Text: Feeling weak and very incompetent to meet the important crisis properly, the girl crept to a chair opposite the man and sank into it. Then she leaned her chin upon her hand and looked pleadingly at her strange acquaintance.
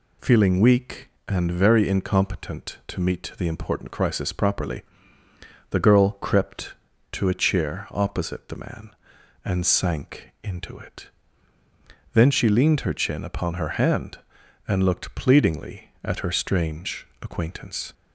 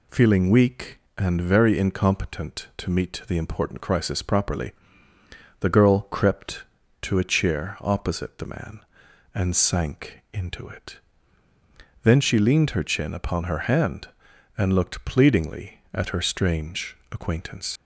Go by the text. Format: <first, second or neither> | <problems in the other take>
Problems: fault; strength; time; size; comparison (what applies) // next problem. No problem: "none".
first | pauses between "strange" and "acquaintance"; slight; at 16.9 s; 0.16 s long; slight in the first // leaves "acquaintance" unfinished; at 17.7 s; 70 ms